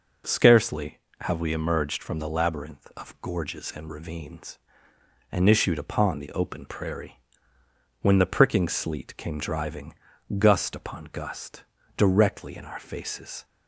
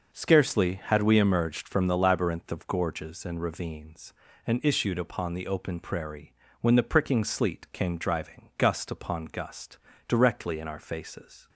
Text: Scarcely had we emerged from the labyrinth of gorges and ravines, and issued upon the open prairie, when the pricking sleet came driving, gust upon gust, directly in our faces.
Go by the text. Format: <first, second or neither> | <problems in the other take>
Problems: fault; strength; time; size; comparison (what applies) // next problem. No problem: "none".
second | says "have" for "had"; at 1.2 s